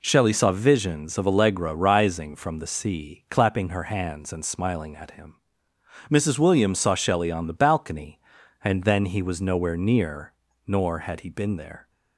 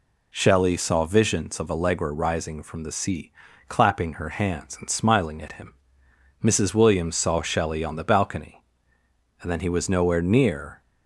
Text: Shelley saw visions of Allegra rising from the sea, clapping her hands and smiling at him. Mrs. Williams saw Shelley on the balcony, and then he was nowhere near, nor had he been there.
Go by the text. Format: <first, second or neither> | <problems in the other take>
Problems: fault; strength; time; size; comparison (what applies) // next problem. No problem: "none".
first | stops before "nor had he been there"; at 10.8 s